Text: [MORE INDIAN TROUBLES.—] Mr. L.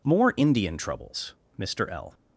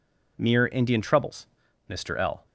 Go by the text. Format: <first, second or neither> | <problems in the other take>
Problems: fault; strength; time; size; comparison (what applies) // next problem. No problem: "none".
first | says "Mere" for "MORE"; at 0.3 s